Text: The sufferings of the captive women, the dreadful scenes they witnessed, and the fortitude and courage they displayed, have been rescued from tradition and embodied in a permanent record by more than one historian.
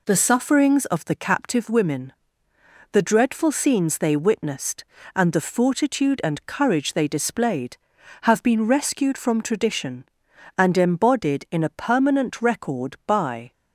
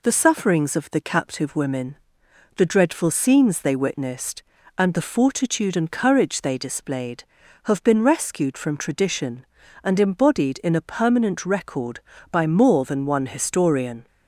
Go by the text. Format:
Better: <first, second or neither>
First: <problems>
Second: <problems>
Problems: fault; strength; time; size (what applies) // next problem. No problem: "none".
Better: second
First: stops before "more than one historian"; at 13.5 s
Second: none